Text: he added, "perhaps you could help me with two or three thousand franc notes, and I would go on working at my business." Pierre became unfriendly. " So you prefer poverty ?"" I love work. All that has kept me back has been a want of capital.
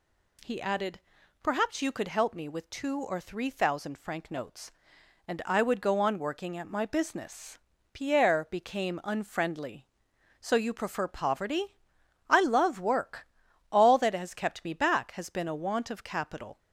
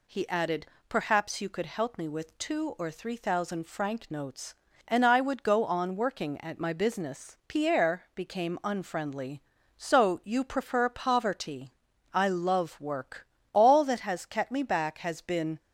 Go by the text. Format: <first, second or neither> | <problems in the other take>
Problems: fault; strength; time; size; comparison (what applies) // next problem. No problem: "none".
first | stops before "a want of capital"; at 15.5 s